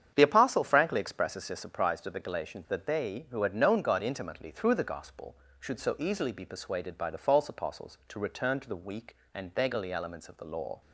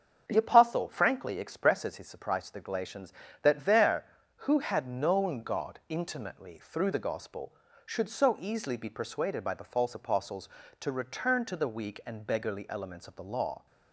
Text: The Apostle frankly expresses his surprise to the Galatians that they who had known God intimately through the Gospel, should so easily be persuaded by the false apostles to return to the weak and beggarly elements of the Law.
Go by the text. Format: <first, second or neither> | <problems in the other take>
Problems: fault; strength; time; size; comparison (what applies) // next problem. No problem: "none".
first | starts louder than the rest; strong; until 1.2 s; 7 dB; strong in the first // says "there" for "they"; at 3.6 s